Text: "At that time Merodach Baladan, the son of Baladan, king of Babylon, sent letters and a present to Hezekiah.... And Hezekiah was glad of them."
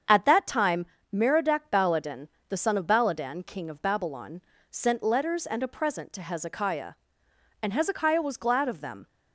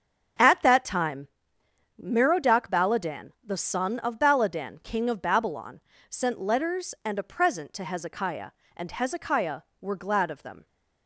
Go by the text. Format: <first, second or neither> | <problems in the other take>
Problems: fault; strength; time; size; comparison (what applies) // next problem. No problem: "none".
first | starts louder than the rest; until 2.1 s; 7 dB; strong in the first // pauses between "time" and "Merodach"; noticeable; at 1.2 s; 0.72 s long; slight in the first // says "were" for "was"; at 9.8 s